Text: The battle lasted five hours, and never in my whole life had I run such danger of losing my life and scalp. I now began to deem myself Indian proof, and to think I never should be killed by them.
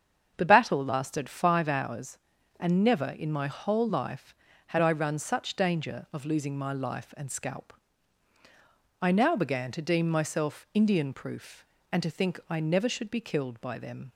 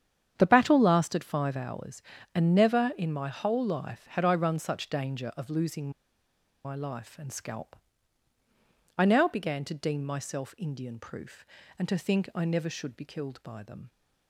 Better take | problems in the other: first | starts louder than the rest; strong; until 1.3 s; 8.5 dB; strong in the first // pauses between "losing" and "my"; noticeable; at 5.8 s; 0.75 s long

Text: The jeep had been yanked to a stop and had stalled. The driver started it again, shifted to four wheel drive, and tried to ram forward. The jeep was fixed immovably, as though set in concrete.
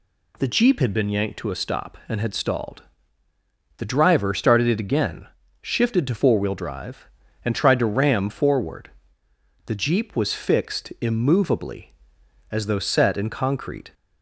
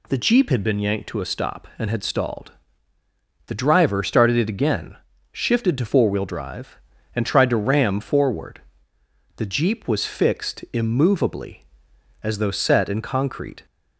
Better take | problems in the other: neither | none

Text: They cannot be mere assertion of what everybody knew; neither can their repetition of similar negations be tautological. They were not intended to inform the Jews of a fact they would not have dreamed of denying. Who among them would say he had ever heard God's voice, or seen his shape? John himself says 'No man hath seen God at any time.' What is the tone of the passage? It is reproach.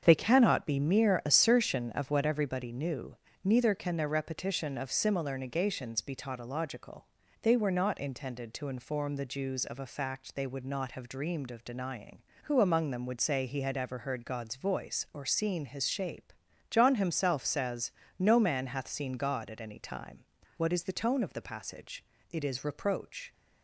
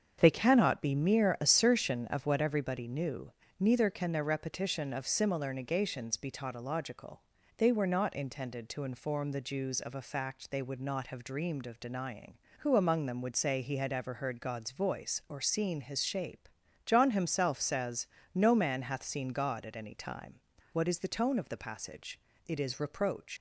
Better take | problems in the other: first | starts louder than the rest; strong; until 1.2 s; 7 dB; strong in the first // pauses between "says" and "No"; slight; at 18.0 s; 0.30 s long; slight in the first // leaves "reproach" unfinished; at 23.3 s; 105 ms

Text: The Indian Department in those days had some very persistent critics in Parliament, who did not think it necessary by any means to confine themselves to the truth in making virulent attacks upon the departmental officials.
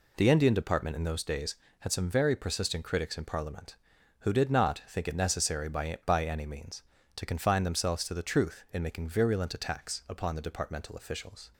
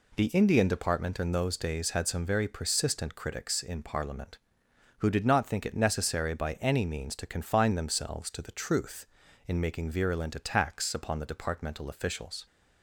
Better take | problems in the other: second | says "by" twice; at 6.0 s

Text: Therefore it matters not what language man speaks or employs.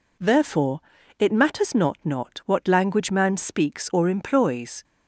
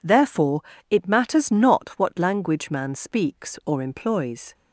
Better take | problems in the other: second | pauses between "Therefore" and "it"; at 0.7 s; 0.38 s long; slight in the second // says "not" twice; at 2.0 s

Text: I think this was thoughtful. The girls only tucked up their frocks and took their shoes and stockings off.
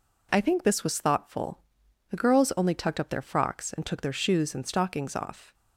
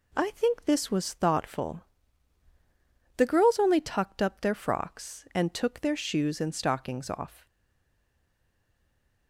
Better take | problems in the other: first | stays silent after the last word; noticeable; from 7.4 s on; 1.8 s long

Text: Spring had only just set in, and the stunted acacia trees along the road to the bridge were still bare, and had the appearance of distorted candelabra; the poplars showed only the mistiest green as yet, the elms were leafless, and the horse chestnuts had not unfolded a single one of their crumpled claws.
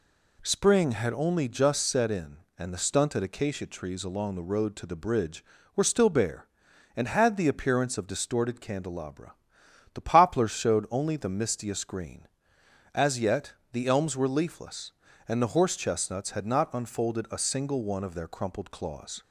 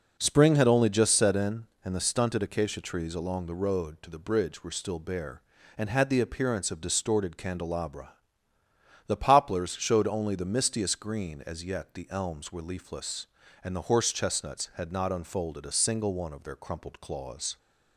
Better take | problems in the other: first | starts louder than the rest; noticeable; until 1.4 s; 5 dB

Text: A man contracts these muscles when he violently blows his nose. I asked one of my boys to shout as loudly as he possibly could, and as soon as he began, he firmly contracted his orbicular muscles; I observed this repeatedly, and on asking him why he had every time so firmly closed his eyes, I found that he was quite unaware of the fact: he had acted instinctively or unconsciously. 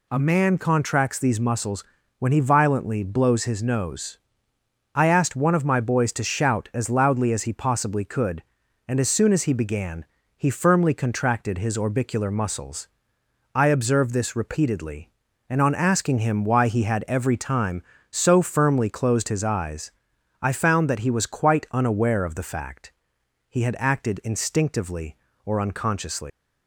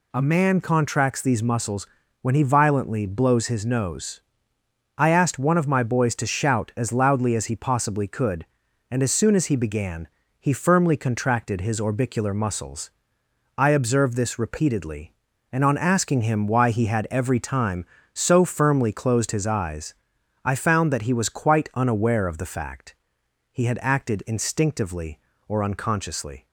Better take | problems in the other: second | pauses between "muscles" and "when"; at 1.8 s; 0.38 s long; also in the second // leaves "unconsciously" unfinished; at 26.3 s; 140 ms

